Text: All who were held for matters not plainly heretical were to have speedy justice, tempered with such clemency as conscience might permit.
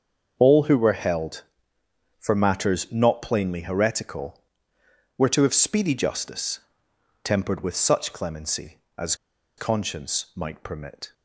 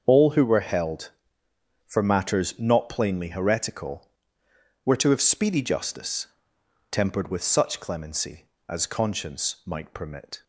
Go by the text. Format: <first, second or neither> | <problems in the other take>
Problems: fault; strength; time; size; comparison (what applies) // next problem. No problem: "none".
second | starts louder than the rest; until 1.3 s; 7 dB; also in the second // pauses between "as" and "conscience"; at 9.1 s; 0.43 s long